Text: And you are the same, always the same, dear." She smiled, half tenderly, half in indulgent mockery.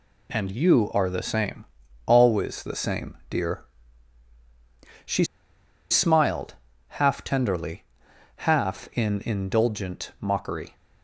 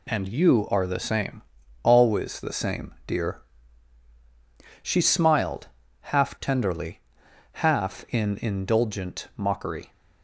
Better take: second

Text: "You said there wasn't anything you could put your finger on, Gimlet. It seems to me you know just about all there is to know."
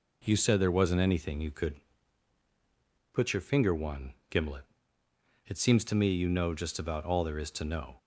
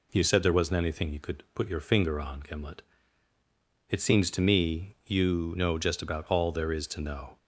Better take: second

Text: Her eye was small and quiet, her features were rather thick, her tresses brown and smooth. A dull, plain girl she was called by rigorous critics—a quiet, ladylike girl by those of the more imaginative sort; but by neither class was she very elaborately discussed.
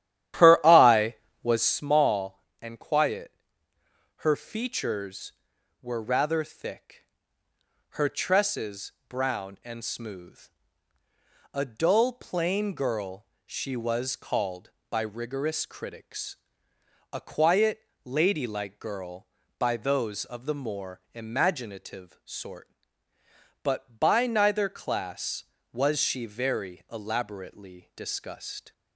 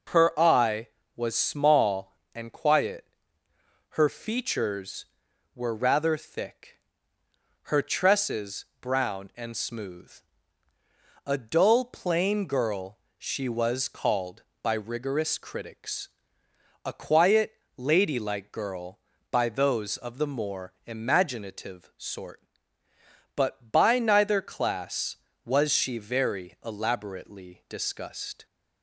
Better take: second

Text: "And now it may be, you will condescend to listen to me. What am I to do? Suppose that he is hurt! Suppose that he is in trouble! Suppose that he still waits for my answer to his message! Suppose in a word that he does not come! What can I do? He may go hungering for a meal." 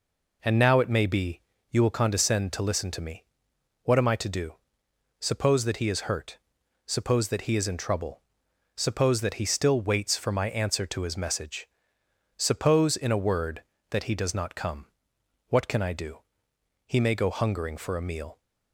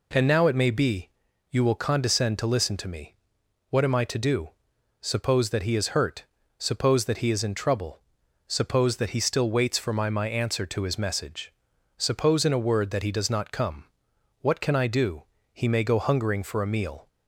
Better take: first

